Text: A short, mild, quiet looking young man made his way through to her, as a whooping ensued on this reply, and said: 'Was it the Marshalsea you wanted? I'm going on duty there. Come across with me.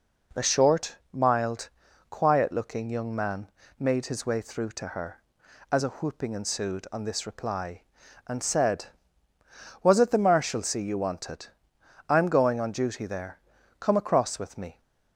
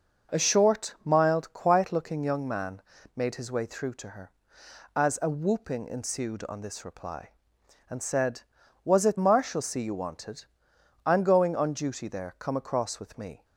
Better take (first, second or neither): first